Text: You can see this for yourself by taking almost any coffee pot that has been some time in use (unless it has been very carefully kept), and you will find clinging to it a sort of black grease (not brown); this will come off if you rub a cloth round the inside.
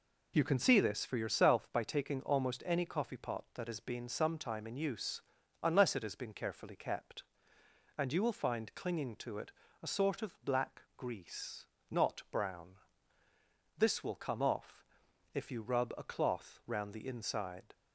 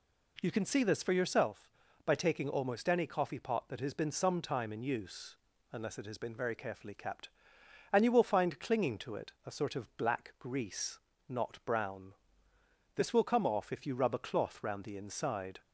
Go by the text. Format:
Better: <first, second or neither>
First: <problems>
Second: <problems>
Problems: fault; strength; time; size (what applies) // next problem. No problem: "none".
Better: second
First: skips "very"; at 6.3 s // pauses between "it" and "a"; slight; at 9.5 s; 0.28 s long // pauses between "off" and "if"; noticeable; at 14.8 s; 0.50 s long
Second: pauses between "it" and "a"; slight; at 9.3 s; 0.16 s long